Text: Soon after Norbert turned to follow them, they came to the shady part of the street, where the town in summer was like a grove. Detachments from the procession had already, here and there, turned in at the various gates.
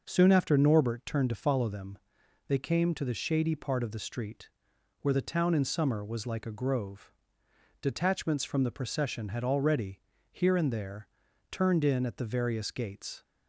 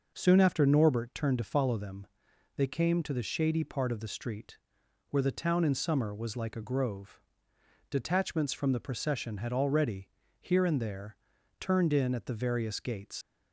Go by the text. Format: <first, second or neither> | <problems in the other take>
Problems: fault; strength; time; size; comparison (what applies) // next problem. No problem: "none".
first | leaves "gates" unfinished; at 13.2 s; 105 ms